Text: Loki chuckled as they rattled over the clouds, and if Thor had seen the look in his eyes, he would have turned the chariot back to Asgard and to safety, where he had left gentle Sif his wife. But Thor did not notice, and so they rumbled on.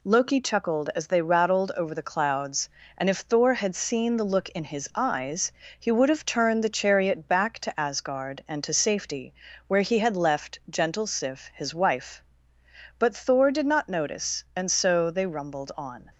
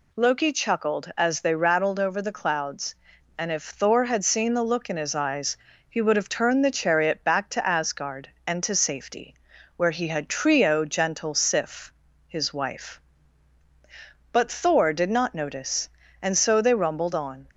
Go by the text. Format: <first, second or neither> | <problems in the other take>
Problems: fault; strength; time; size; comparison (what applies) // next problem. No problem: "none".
first | says "trio" for "left"; at 10.2 s // pauses between "Sif" and "his"; slight; at 11.9 s; 0.34 s long